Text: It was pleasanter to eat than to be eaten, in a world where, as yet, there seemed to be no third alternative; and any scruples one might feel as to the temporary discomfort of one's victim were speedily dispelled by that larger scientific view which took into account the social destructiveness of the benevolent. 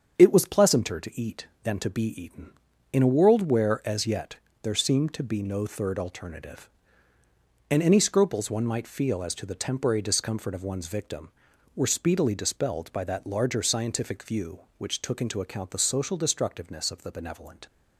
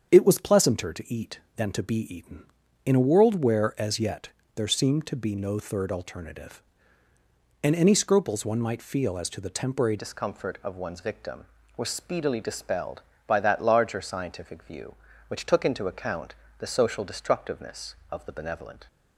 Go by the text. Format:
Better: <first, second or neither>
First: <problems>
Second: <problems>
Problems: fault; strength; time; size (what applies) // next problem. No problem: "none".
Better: first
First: starts louder than the rest; strong; until 1.1 s; 7.5 dB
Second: starts louder than the rest; strong; until 1.1 s; 7.5 dB // changes voice at "discomfort"; from 9.9 s on; 8.9 s long // pauses between "account" and "the"; slight; at 16.3 s; 0.24 s long